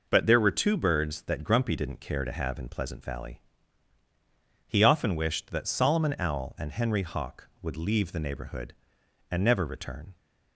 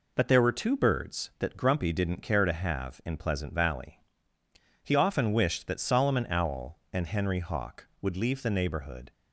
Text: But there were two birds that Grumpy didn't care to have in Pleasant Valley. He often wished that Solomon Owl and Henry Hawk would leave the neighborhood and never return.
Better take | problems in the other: first | stops before "and never return"; at 9.1 s

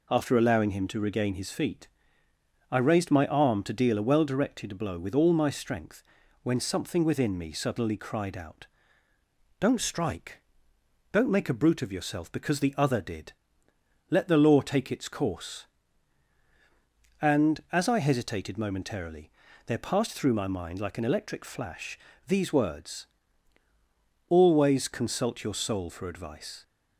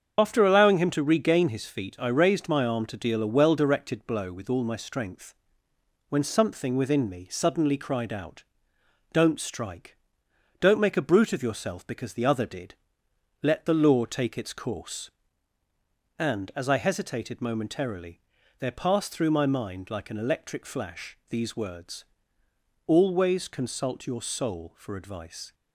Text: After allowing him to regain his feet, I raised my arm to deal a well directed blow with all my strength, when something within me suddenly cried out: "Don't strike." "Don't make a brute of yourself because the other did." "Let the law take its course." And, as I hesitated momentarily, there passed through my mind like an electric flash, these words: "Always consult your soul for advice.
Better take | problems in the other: first | loses the start of "After"; at 0.1 s; 50 ms // starts louder than the rest; until 1.1 s; 7 dB

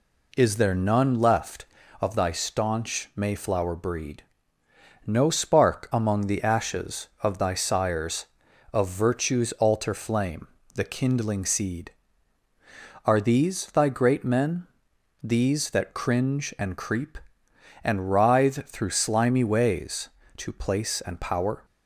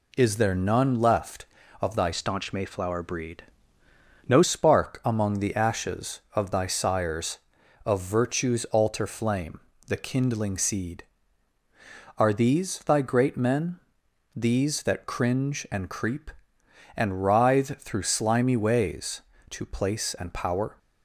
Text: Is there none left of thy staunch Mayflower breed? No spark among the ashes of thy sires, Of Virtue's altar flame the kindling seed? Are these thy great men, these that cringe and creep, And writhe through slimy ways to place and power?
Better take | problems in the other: first | changes voice from "staunch" to "No"; from 2.1 to 4.4 s; 2.3 s long // pauses between "flame" and "the"; slight; at 9.5 s; 0.26 s long; slight in the first

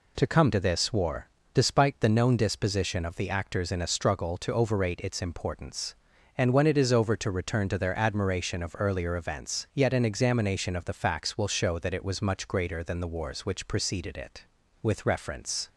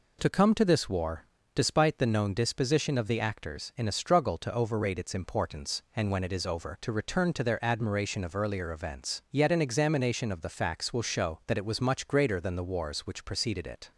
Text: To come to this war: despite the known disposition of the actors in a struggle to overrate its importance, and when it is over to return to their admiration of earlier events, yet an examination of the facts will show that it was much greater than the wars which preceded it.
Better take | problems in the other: second | goes on to say "With reference"; noticeable; from 14.8 s on; 0.86 s long

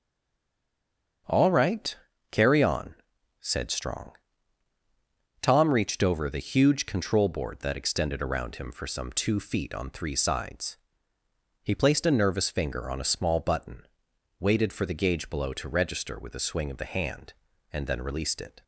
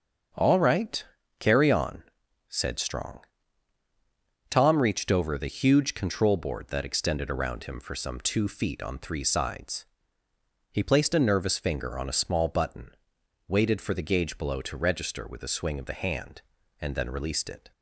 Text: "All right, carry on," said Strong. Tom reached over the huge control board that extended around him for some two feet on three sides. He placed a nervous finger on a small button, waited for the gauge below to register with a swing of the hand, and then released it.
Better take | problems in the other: second | stays silent before the first word; noticeable; until 1.2 s; 1.2 s long // starts louder than the rest; until 2.6 s; 7 dB; also in the second

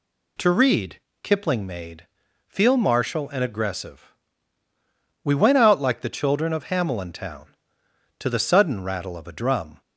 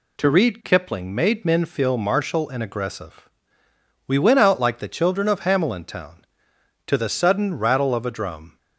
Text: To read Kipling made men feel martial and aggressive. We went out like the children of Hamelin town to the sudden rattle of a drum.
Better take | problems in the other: second | pauses between "read" and "Kipling"; slight; at 0.9 s; 0.24 s long // skips "men"; at 2.2 s

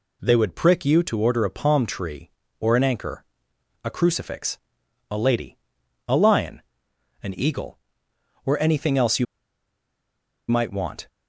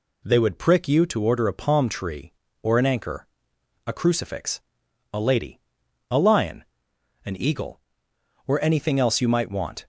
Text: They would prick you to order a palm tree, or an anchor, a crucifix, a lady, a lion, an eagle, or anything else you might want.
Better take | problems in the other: second | pauses between "you" and "might"; strong; at 9.2 s; 1.2 s long

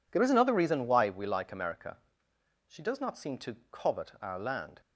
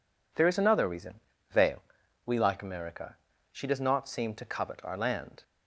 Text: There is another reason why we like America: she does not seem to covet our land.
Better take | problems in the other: first | says "veil" for "why"; at 1.5 s

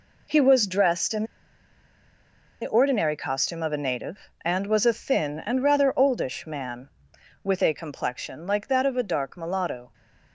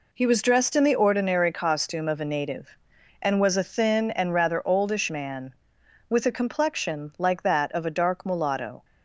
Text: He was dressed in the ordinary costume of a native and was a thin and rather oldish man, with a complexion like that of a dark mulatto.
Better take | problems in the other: second | pauses between "in" and "the"; strong; at 1.2 s; 1.3 s long

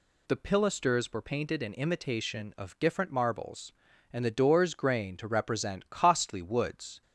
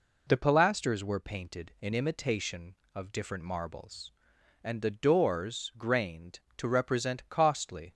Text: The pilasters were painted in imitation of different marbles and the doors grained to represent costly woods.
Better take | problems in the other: first | stops before "woods"; at 7.9 s

